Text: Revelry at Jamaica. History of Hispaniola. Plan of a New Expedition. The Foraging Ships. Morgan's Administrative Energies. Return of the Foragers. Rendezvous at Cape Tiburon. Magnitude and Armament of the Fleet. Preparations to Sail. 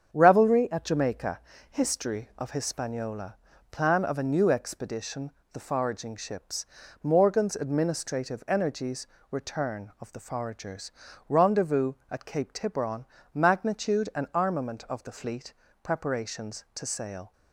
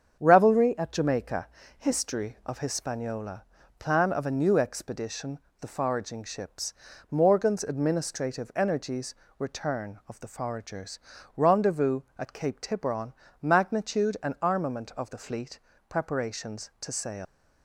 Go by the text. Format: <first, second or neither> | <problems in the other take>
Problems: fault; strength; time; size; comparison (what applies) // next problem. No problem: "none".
first | starts louder than the rest; strong; until 1.2 s; 7.5 dB; strong in the first // leaves "Sail" unfinished; at 17.2 s; 130 ms